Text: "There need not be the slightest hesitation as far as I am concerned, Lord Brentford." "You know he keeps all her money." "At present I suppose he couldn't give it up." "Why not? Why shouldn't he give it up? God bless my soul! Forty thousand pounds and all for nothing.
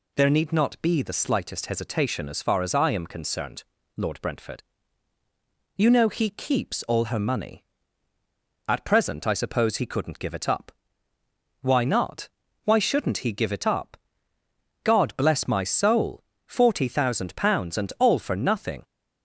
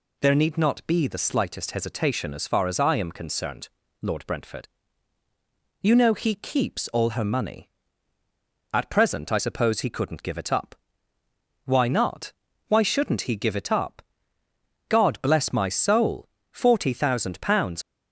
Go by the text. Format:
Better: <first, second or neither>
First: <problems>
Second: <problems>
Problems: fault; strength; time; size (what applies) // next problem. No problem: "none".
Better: first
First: none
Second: stops before "and all for nothing"; at 17.8 s